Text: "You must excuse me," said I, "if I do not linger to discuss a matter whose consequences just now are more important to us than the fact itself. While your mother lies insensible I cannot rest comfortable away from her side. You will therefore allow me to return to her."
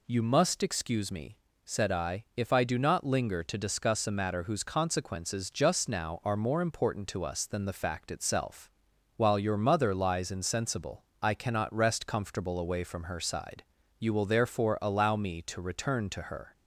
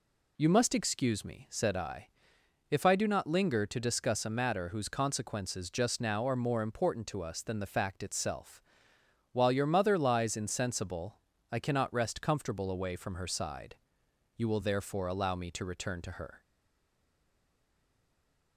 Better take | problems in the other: first | pauses between "insensible" and "I"; slight; at 11.2 s; 0.32 s long; slight in the first // stays silent after the last word; from 16.4 s on; 2.1 s long

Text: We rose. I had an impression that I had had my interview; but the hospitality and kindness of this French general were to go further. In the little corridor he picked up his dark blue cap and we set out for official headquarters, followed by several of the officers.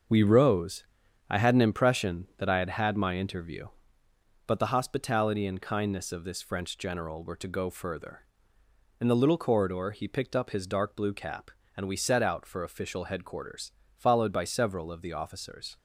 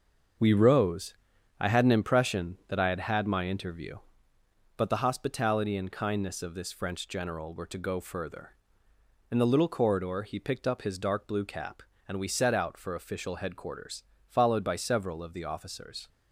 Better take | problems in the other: neither | starts louder than the rest; the same in both

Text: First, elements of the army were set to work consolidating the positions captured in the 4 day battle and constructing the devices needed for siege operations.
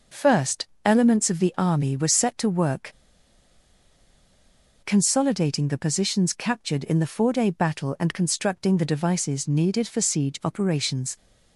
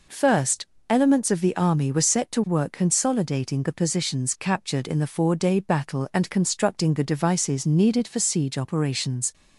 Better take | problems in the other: second | pauses between "work" and "consolidating"; strong; at 2.9 s; 1.9 s long

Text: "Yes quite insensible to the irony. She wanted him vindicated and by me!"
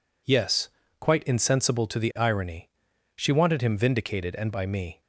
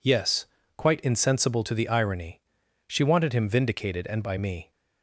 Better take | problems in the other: neither | pauses between "Yes" and "quite"; slight; the same in both

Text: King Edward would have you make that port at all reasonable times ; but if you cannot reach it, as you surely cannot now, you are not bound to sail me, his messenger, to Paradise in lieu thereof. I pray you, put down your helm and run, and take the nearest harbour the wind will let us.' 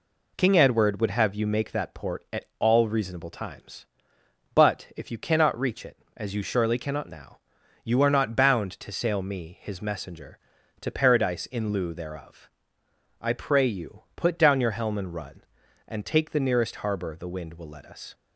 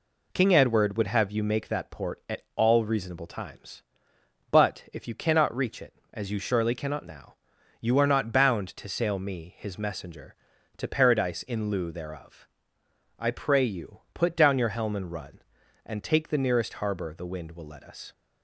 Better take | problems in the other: neither | none

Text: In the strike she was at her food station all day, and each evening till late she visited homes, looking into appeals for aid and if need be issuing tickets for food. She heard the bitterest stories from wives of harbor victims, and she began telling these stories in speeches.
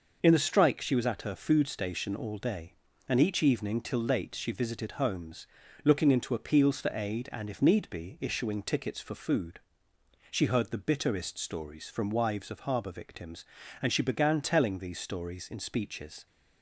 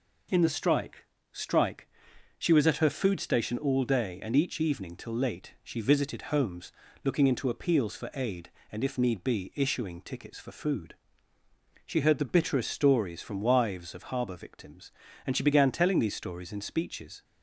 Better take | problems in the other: first | says "strike" twice; at 1.3 s

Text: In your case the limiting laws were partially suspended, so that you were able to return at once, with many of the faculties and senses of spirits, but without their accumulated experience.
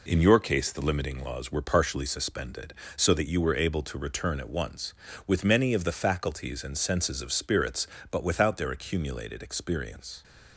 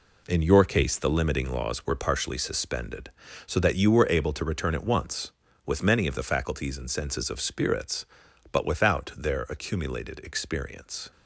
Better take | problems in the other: first | gets quieter; strong; throughout; 7.5 dB

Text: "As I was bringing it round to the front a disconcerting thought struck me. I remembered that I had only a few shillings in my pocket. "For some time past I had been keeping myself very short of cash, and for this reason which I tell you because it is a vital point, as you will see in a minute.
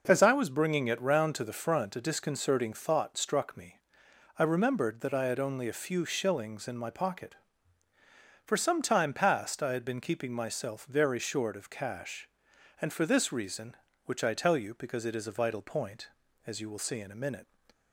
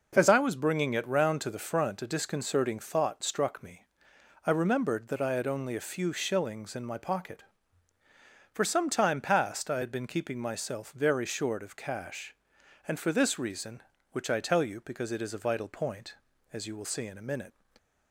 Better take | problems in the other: neither | none

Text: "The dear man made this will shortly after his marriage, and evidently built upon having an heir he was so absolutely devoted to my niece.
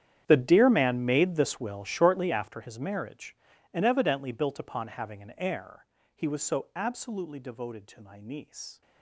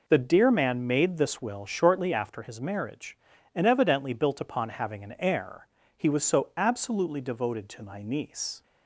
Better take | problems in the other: second | gets quieter; strong; throughout; 18.5 dB // pauses between "heir" and "he"; slight; at 5.8 s; 0.30 s long; slight in the second

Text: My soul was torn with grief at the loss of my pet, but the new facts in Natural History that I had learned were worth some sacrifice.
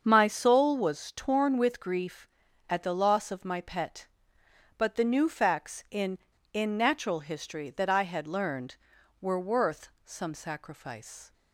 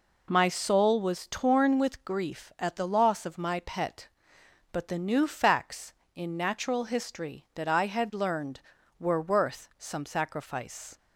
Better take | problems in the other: second | starts louder than the rest; until 1.0 s; 7 dB // says "in" twice; at 6.5 s // pauses between "worth" and "some"; slight; at 9.8 s; 0.16 s long

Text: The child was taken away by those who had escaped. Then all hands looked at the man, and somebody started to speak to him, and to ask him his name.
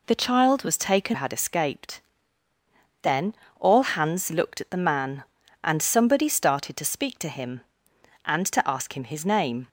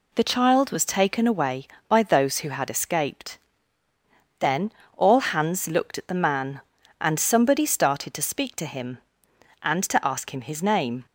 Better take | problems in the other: second | skips "away by those who"; at 1.1 s // pauses between "Then" and "all"; slight; at 3.3 s; 0.26 s long; slight in the second

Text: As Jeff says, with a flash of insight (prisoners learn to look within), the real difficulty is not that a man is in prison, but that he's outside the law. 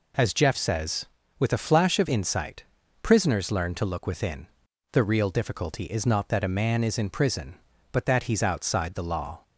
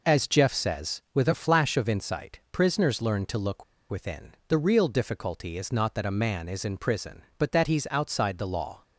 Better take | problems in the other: first | pauses between "look" and "within"; slight; at 3.6 s; 0.26 s long

